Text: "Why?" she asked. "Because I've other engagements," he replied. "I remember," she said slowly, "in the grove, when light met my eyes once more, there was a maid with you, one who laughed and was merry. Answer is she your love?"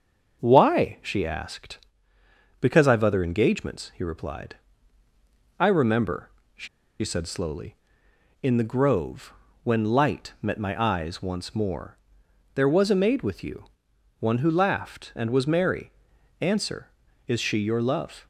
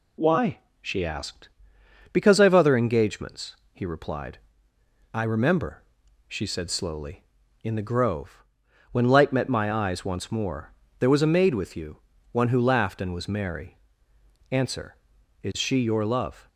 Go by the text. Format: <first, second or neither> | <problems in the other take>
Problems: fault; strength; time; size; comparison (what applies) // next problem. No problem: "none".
second | starts louder than the rest; until 1.4 s; 6.5 dB // pauses between "she" and "said"; slight; at 6.6 s; 0.34 s long